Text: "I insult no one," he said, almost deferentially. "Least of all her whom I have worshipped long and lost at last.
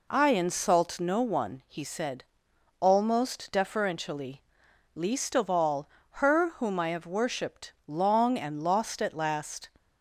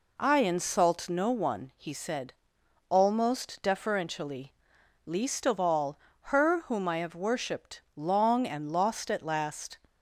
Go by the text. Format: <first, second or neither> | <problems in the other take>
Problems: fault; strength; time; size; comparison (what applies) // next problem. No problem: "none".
neither | pauses between "all" and "her"; slight; the same in both